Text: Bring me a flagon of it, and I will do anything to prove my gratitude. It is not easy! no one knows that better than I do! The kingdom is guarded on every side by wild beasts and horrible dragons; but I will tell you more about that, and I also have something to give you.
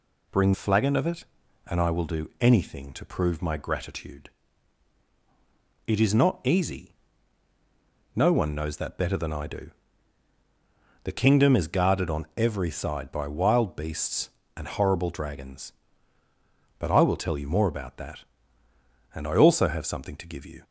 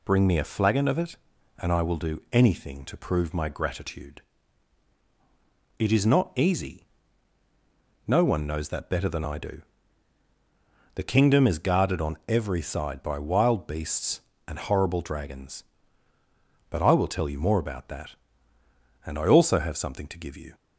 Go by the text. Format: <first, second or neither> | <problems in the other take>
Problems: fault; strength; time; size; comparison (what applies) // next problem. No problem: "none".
second | skips "me a"; at 0.5 s